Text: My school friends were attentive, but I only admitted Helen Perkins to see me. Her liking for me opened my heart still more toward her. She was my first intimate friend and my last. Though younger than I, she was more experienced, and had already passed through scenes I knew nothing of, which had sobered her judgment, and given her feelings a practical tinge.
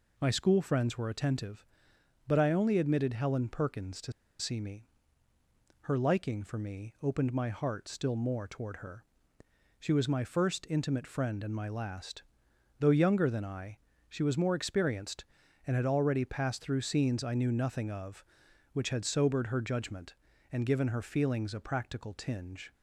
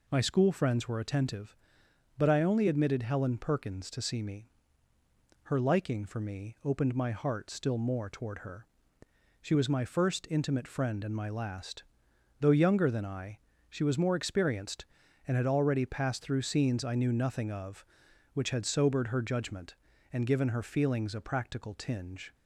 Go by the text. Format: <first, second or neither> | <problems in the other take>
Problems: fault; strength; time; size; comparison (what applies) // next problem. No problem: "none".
second | pauses between "to" and "see"; slight; at 4.1 s; 0.27 s long